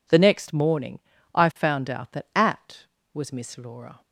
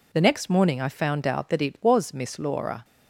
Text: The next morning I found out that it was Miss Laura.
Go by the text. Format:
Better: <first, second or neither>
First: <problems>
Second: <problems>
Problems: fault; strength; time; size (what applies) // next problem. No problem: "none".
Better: second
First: pauses between "morning" and "I"; slight; at 0.9 s; 0.36 s long // says "at" for "it"; at 2.3 s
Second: none